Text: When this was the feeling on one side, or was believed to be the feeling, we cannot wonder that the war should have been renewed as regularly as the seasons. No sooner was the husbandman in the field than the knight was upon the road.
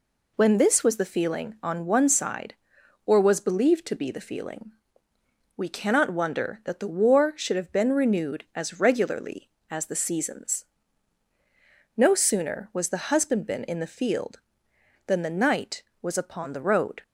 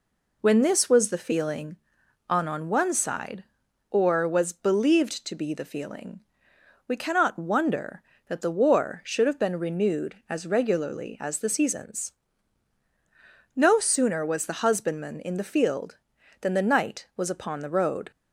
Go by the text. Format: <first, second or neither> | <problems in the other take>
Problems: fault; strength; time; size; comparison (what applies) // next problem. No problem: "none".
first | says "on" twice; at 2.4 s